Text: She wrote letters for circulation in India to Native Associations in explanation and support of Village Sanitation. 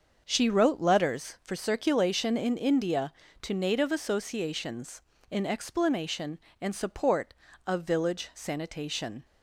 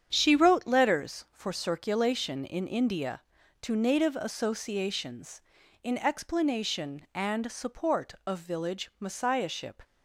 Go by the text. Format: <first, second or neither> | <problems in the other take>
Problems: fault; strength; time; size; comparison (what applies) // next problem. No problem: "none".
first | starts louder than the rest; strong; until 1.1 s; 8.5 dB; also in the first // says "Messiahship" for "Sanitation"; at 8.9 s